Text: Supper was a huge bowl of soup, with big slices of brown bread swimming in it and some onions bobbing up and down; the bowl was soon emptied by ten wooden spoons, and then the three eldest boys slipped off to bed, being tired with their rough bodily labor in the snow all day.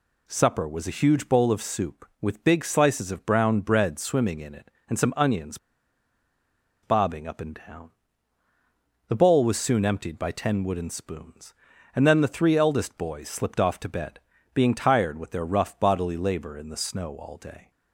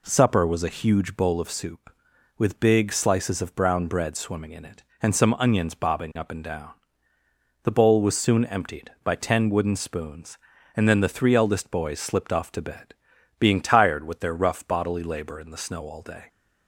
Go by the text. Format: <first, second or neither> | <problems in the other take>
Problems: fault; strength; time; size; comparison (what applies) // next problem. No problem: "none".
second | pauses between "onions" and "bobbing"; strong; at 5.5 s; 1.2 s long